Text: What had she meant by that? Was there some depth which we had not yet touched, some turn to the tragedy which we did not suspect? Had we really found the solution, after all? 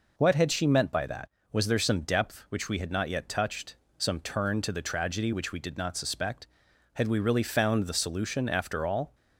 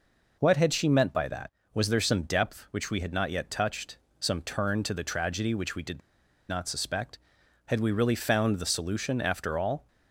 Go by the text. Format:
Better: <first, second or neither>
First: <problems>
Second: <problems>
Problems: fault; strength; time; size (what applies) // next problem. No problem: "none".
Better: first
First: none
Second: pauses between "did" and "not"; noticeable; at 5.9 s; 0.49 s long